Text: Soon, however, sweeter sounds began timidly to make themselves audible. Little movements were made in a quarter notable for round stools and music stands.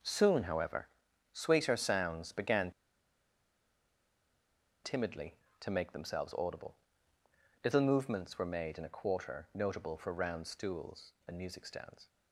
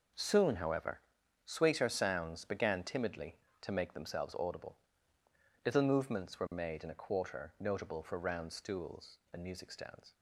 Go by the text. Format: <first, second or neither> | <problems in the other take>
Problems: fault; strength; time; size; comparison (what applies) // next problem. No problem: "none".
second | pauses between "began" and "timidly"; strong; at 2.7 s; 2.1 s long